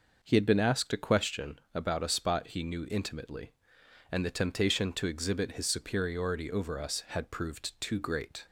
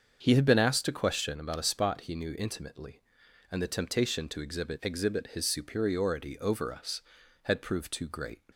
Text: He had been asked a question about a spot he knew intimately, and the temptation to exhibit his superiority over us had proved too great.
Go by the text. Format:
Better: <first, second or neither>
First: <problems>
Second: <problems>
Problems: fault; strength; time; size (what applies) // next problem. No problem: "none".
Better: first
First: none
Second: starts louder than the rest; until 1.2 s; 7 dB // says "exhibit" twice; at 4.8 s